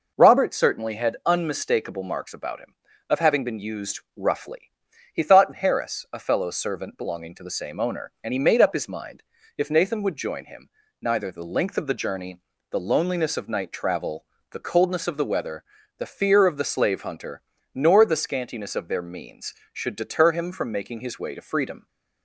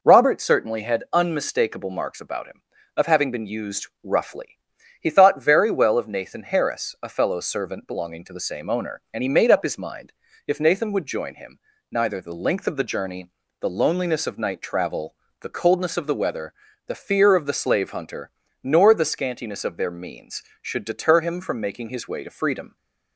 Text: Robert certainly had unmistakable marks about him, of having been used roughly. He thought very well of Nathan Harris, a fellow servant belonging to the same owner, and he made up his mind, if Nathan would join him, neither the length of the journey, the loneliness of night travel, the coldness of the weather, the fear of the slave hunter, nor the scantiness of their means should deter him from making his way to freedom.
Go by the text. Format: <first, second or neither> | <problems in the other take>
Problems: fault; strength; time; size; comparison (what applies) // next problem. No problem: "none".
second | pauses between "used" and "roughly"; slight; at 3.9 s; 0.16 s long; slight in the second // skips "very well of Nathan"; at 5.5 s